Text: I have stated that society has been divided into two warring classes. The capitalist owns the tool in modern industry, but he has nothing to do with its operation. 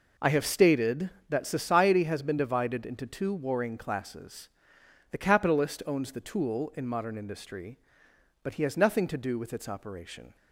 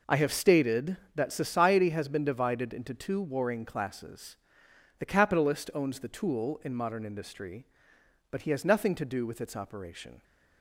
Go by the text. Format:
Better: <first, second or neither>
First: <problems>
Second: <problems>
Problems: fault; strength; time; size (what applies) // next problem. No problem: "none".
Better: neither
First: none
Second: none